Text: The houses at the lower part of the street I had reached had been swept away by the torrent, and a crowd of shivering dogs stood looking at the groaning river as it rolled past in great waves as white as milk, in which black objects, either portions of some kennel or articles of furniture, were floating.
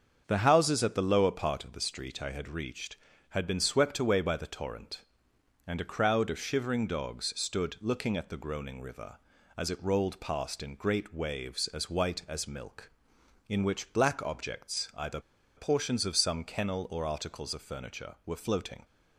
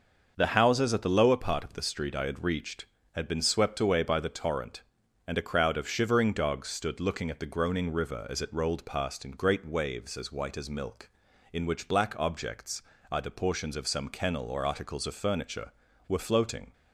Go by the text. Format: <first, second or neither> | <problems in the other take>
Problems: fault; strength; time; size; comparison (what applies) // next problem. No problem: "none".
second | starts louder than the rest; until 1.2 s; 7 dB; also in the second // pauses between "either" and "portions"; at 15.2 s; 0.36 s long